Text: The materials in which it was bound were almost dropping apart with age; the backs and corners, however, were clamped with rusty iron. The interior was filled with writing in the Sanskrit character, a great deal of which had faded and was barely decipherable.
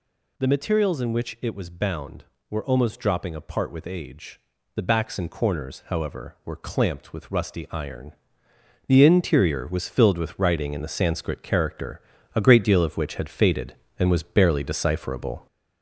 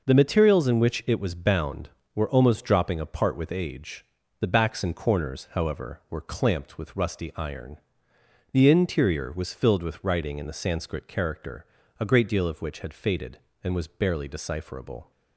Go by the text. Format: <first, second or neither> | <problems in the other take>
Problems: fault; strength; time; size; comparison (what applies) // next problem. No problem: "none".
second | gets louder; throughout; 3.5 dB